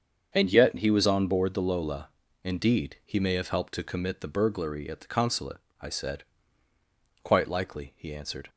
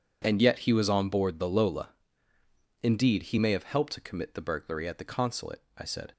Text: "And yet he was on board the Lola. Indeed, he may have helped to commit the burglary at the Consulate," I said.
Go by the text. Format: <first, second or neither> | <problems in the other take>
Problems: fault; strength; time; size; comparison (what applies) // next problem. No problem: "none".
second | starts louder than the rest; until 1.3 s; 7 dB // goes on to say "Quite likely he answered"; noticeable; from 7.2 s on; 1.2 s long